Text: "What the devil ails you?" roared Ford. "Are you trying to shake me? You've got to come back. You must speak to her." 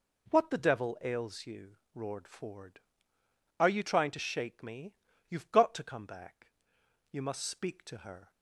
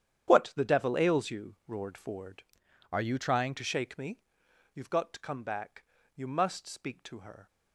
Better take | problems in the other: first | starts louder than the rest; strong; until 1.3 s; 9.5 dB // changes voice from "Are" to "trying"; from 2.9 to 3.5 s; 0.6 s long

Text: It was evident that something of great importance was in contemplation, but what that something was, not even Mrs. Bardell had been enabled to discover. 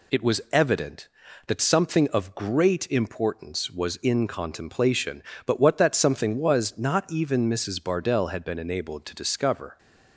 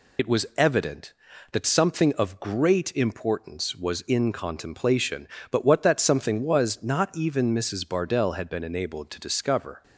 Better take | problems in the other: first | loses the start of "It"; at 0.1 s; 25 ms

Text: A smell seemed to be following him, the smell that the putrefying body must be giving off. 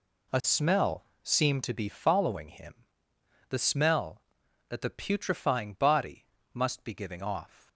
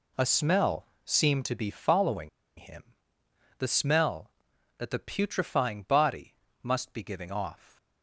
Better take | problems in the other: first | pauses between "smell" and "seemed"; slight; at 0.8 s; 0.18 s long; slight in the first // pauses between "following" and "him"; slight; at 2.2 s; 0.27 s long // pauses between "body" and "must"; slight; at 6.3 s; 0.30 s long; slight in the first

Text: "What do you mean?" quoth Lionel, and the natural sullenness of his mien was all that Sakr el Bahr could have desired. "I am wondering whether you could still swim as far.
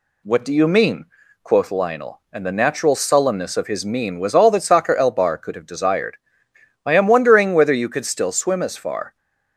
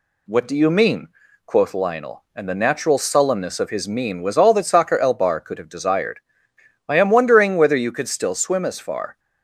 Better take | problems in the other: neither | none

